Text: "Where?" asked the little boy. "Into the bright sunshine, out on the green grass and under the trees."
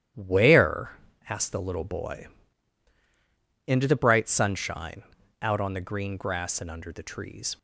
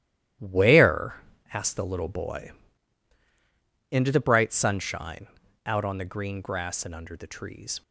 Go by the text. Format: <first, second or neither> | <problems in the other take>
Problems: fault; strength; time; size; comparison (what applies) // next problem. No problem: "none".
first | gets quieter; strong; throughout; 10.5 dB // starts louder than the rest; strong; until 1.7 s; 12.5 dB; strong in the first